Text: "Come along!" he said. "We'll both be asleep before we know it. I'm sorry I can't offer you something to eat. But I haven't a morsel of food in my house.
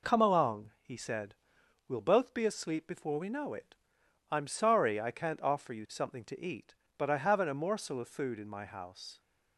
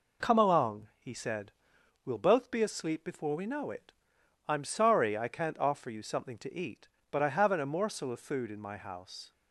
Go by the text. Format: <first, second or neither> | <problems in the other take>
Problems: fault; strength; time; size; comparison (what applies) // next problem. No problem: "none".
neither | none